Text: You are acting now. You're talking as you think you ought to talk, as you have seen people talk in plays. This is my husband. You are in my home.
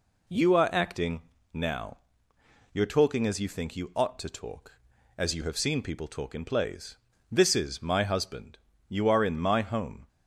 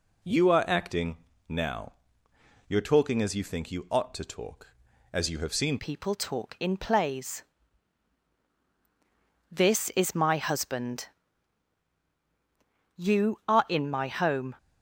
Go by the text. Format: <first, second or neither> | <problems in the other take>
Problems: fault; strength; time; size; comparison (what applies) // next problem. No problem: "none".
first | pauses between "acting" and "now"; slight; at 1.1 s; 0.32 s long; slight in the first // changes voice at "people"; from 5.7 s on; 8.8 s long